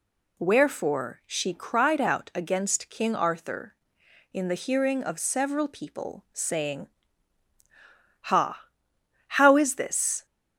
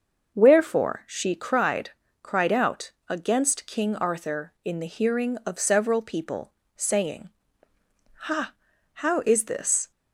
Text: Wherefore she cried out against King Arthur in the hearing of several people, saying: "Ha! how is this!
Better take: first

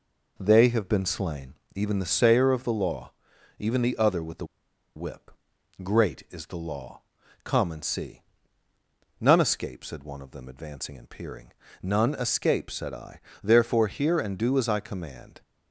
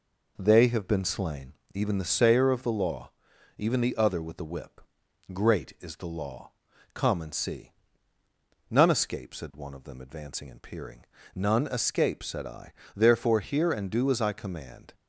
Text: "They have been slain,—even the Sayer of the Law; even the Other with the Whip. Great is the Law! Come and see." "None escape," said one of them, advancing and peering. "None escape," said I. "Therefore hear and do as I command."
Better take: second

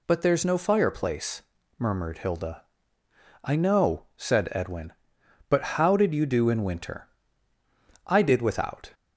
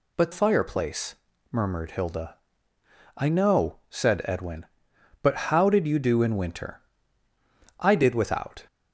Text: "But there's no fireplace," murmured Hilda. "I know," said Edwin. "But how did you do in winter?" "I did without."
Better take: first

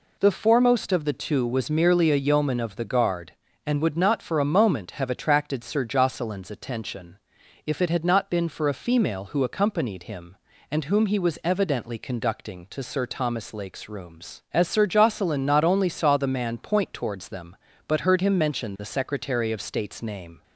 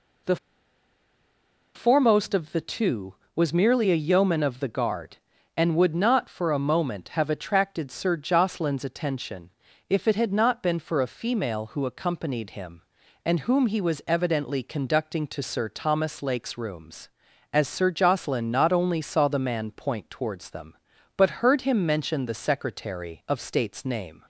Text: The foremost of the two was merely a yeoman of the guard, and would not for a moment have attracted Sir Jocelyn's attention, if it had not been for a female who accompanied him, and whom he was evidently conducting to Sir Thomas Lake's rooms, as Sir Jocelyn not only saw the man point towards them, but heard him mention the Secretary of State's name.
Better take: first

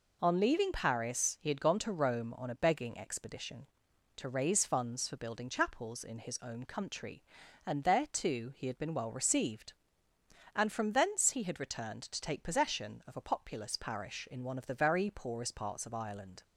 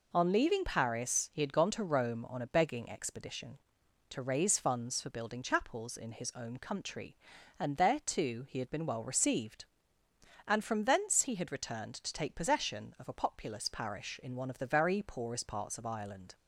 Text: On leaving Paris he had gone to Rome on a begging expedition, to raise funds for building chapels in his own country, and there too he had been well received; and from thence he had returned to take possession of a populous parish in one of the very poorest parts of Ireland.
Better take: neither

